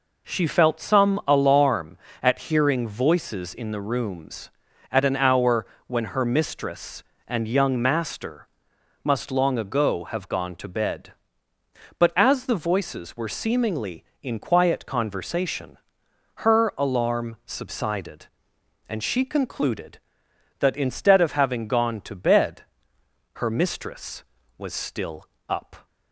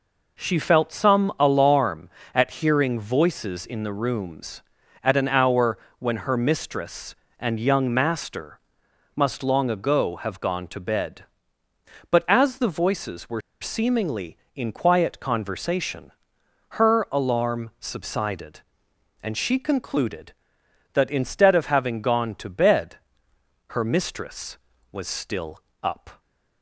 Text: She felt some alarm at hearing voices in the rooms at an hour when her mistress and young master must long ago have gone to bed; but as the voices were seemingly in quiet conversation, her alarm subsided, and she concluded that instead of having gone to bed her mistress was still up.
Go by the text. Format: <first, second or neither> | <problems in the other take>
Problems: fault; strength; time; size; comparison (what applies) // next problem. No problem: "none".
first | pauses between "hour" and "when"; slight; at 5.7 s; 0.18 s long; slight in the first // pauses between "master" and "must"; noticeable; at 8.5 s; 0.56 s long; noticeable in the first // pauses between "were" and "seemingly"; slight; at 13.4 s; 0.21 s long // pauses between "bed" and "her"; noticeable; at 22.9 s; 0.72 s long; noticeable in the first // pauses between "still" and "up"; slight; at 25.6 s; 0.22 s long; slight in the first